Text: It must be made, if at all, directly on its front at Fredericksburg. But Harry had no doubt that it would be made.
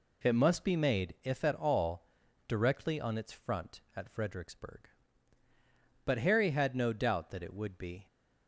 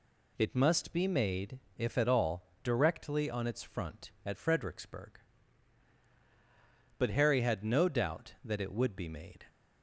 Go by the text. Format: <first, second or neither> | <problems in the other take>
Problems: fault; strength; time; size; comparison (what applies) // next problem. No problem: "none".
second | stops before "made"; at 8.0 s